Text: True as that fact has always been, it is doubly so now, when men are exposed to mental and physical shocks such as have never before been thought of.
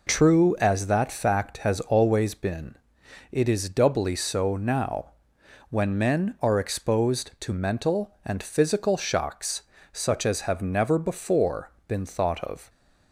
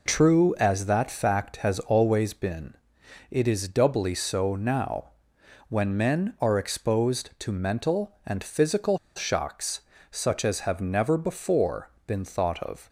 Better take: first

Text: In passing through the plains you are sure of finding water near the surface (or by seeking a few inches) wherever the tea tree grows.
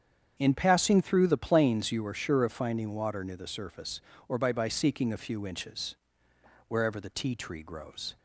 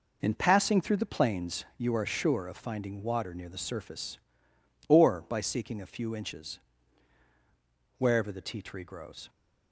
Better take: second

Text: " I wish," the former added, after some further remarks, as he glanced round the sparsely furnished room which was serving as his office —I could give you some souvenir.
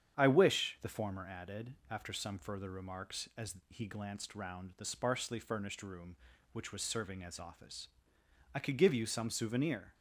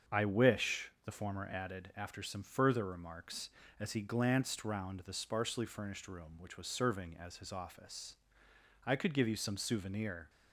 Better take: second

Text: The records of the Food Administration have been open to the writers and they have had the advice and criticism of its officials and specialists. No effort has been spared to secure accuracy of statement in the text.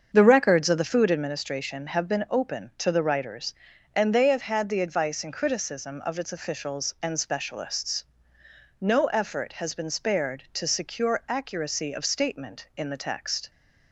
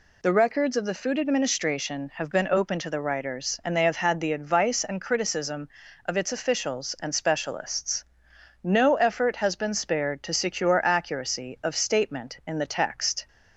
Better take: second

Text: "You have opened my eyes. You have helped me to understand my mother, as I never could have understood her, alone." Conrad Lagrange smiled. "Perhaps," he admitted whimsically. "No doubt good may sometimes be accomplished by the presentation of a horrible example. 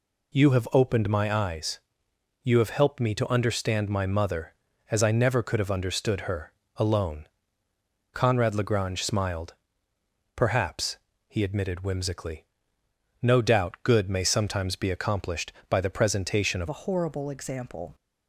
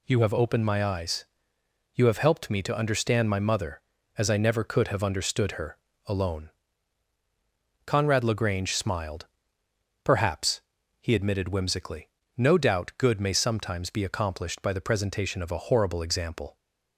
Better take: second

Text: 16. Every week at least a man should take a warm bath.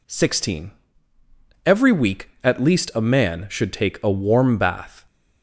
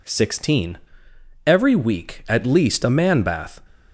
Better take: first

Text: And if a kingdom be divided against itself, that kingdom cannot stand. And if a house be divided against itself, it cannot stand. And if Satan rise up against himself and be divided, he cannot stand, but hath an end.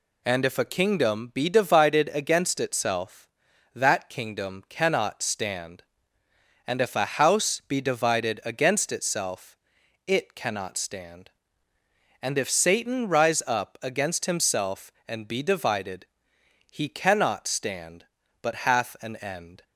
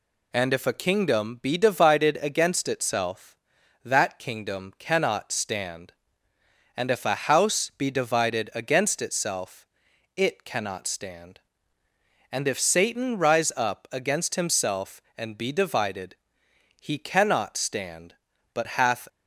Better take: first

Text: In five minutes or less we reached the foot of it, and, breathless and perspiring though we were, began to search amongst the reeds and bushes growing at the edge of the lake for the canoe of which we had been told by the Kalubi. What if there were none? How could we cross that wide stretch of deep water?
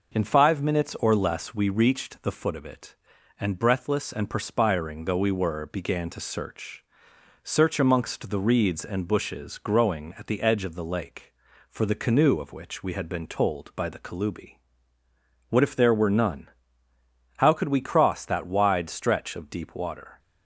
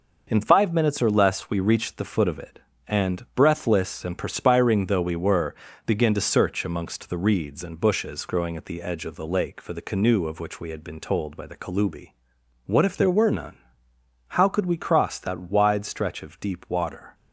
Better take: second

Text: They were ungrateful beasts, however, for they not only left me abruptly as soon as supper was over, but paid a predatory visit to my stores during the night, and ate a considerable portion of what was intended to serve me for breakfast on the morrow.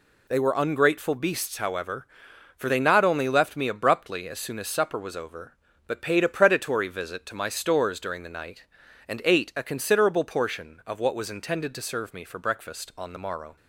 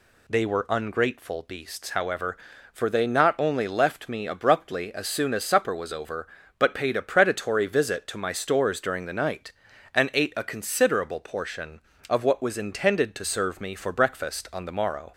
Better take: neither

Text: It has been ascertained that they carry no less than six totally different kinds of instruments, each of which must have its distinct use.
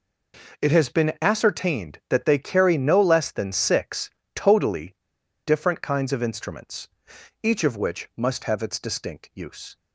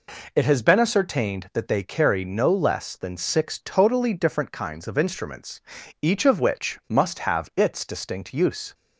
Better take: second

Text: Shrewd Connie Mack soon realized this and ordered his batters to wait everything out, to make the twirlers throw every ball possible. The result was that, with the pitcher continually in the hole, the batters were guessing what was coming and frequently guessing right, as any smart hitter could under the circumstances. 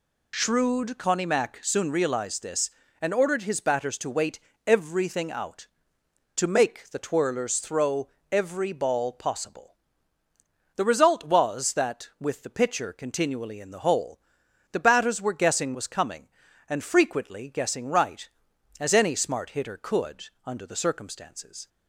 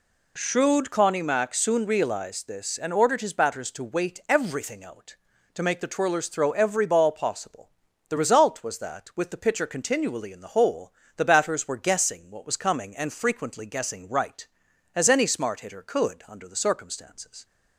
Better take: second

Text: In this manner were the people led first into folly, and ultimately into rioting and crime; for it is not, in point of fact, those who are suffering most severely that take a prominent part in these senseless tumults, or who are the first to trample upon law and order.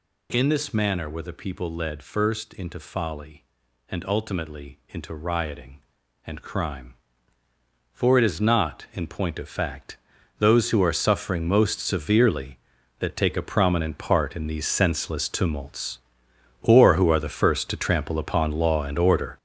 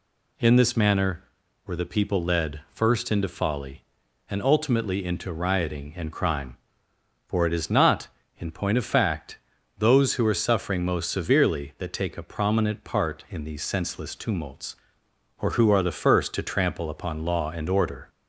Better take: second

